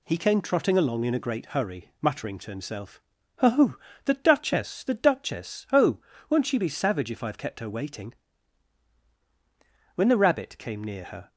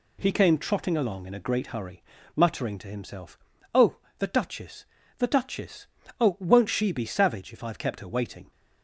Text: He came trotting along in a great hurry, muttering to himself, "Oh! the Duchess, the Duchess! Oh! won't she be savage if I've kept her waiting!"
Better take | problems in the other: second | goes on to say "When the Rabbit came near her"; from 9.9 s on; 1.3 s long

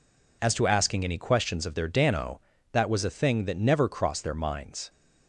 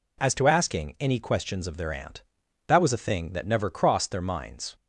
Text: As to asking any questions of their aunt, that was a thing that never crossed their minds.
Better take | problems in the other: second | says "dano" for "aunt"; at 1.8 s

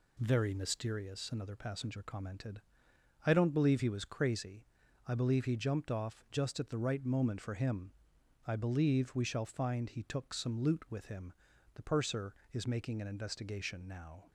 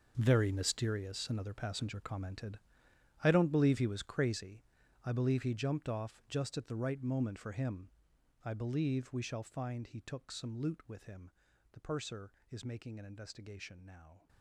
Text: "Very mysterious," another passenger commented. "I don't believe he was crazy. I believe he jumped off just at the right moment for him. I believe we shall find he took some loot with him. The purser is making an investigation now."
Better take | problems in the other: first | gets quieter; strong; throughout; 15.5 dB

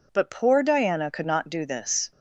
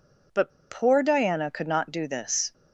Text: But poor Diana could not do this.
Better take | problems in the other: first | pauses between "But" and "poor"; slight; at 0.5 s; 0.19 s long

